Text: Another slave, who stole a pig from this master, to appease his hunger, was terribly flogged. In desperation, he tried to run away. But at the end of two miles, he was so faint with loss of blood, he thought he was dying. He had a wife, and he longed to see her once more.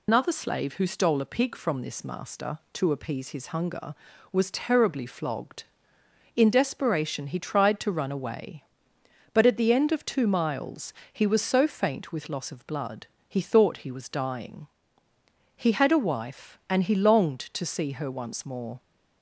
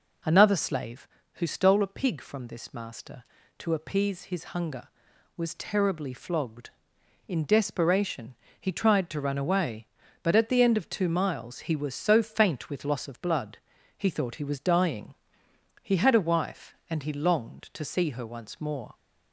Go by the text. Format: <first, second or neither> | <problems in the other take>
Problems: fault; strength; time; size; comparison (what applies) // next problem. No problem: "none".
second | loses the start of "Another"; at 0.0 s; 90 ms